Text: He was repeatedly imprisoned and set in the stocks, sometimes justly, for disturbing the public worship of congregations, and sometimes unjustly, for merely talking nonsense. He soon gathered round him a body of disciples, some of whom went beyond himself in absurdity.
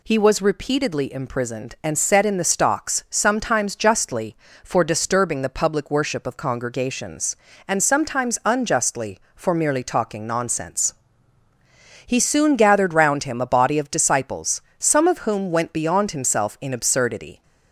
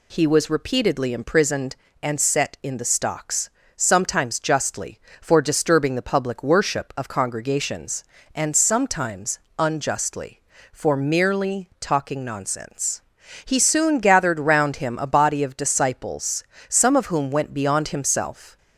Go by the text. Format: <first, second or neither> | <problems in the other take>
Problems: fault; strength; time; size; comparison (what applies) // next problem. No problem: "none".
first | pauses between "sometimes" and "unjustly"; slight; at 9.3 s; 0.18 s long // stops before "in absurdity"; at 18.5 s